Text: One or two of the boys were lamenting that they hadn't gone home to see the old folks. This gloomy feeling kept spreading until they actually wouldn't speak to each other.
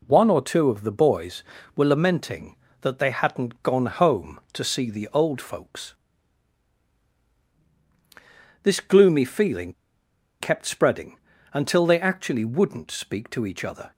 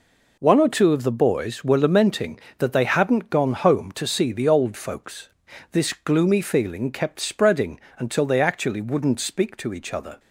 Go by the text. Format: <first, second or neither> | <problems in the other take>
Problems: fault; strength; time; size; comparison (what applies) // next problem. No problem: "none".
second | pauses between "feeling" and "kept"; noticeable; at 9.7 s; 0.69 s long // pauses between "spreading" and "until"; slight; at 11.1 s; 0.36 s long; slight in the second